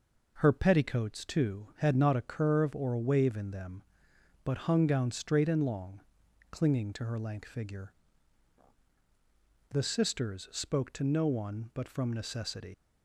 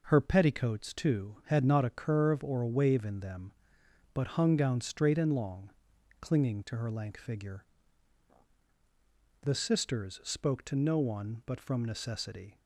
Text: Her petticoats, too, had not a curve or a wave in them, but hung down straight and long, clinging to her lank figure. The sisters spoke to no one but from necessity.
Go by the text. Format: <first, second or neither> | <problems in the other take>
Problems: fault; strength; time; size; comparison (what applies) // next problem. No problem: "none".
second | leaves "necessity" unfinished; at 12.7 s; 110 ms